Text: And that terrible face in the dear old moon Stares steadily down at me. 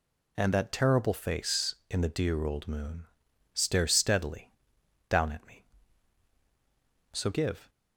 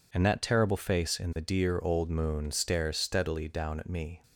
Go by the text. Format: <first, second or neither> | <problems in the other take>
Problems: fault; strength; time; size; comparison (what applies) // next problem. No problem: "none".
second | pauses between "moon" and "Stares"; noticeable; at 3.0 s; 0.52 s long // pauses between "steadily" and "down"; noticeable; at 4.5 s; 0.56 s long // goes on to say "So give"; from 7.1 s on; 0.56 s long